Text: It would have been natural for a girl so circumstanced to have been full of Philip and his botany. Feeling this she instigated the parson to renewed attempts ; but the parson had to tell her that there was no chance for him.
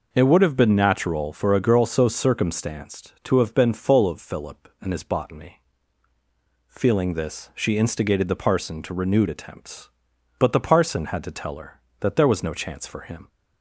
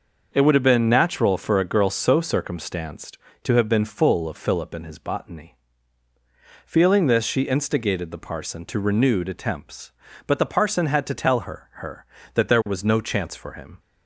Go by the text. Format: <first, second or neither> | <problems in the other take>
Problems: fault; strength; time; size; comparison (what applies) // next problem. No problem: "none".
first | starts louder than the rest; noticeable; until 1.3 s; 6 dB // says "her" twice; at 11.7 s